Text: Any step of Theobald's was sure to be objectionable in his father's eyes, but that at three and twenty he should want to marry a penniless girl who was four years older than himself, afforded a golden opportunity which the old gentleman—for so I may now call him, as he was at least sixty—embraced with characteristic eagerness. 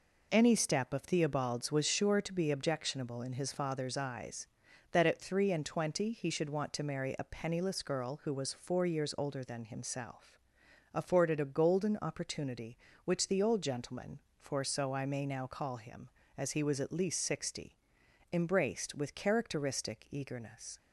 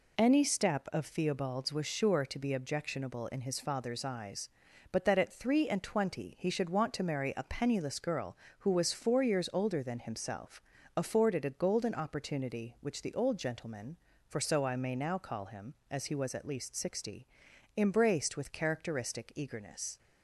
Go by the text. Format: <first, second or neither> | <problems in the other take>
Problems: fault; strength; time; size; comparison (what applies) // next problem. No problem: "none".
second | skips "but"; at 4.6 s